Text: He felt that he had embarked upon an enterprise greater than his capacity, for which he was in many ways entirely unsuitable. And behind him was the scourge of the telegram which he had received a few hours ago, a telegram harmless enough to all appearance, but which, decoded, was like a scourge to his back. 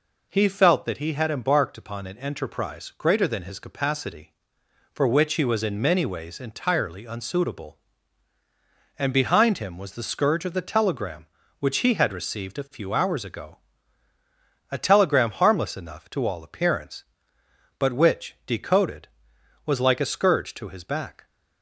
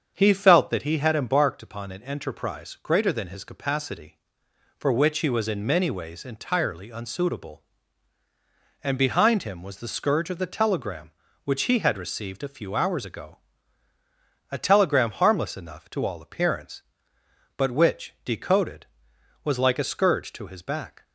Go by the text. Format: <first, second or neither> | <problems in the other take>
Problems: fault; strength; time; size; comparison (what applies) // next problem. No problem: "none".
first | starts louder than the rest; strong; until 1.4 s; 7.5 dB